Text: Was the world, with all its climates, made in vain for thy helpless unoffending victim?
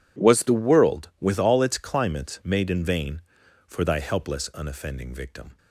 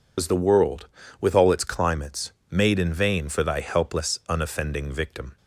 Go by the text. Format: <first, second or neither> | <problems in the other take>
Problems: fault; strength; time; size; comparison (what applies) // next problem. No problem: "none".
first | loses the start of "Was"; at 0.1 s; 90 ms